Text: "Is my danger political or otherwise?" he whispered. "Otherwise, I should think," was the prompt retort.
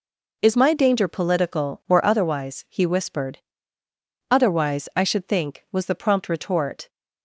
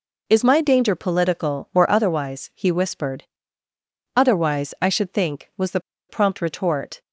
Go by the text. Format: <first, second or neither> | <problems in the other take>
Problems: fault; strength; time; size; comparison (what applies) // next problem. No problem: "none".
first | pauses between "the" and "prompt"; slight; at 5.8 s; 0.28 s long